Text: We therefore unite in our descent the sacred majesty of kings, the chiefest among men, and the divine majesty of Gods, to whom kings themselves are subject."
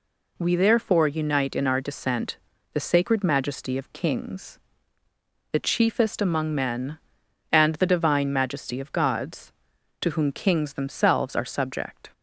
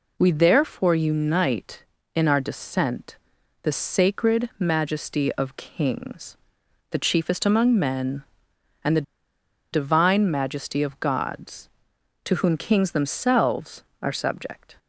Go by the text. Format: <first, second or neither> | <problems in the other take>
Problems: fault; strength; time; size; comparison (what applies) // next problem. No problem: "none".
first | pauses between "descent" and "the"; noticeable; at 3.1 s; 0.46 s long; slight in the first // pauses between "the" and "divine"; noticeable; at 9.0 s; 0.70 s long